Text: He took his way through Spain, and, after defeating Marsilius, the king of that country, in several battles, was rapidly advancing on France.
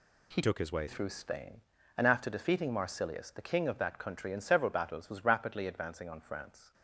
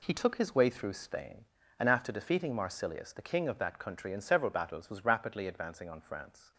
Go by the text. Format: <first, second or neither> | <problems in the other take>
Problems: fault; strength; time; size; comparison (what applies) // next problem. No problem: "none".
second | changes voice from "took" to "way"; from 0.4 to 0.8 s; 0.4 s long